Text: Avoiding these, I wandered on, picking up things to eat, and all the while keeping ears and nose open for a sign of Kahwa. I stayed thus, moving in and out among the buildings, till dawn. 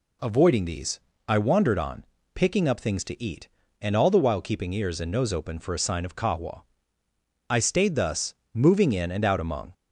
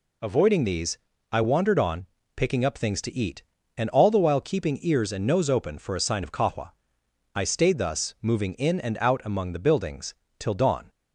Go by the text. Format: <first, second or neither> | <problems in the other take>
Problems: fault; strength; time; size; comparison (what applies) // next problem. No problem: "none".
second | stops before "the buildings till dawn"; at 9.7 s